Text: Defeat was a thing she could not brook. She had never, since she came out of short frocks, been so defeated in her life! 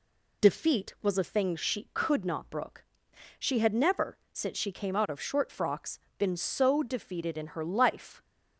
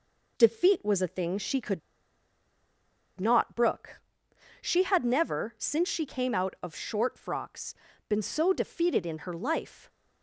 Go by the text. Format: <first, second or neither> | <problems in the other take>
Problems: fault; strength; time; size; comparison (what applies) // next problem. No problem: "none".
first | pauses between "could" and "not"; strong; at 1.8 s; 1.3 s long